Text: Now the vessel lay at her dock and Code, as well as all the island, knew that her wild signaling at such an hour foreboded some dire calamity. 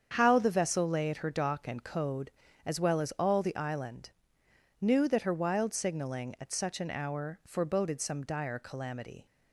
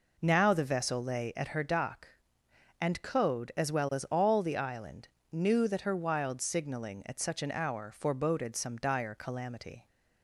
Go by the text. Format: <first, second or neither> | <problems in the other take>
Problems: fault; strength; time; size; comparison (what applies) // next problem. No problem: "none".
second | starts louder than the rest; strong; until 1.1 s; 7.5 dB // says "How" for "Now"; at 0.1 s